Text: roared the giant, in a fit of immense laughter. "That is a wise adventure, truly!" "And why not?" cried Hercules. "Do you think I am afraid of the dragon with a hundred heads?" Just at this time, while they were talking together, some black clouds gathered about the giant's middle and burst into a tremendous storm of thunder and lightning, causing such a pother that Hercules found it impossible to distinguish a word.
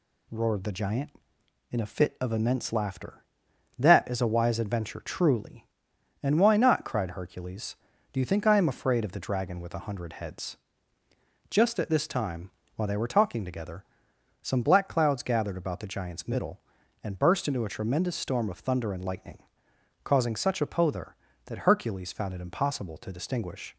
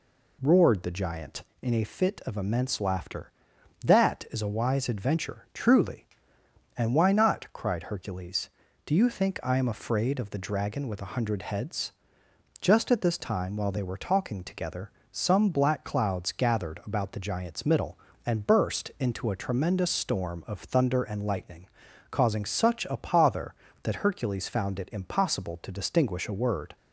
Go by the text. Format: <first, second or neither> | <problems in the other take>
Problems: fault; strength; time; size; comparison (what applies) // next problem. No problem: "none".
second | stops before "a word"; at 23.7 s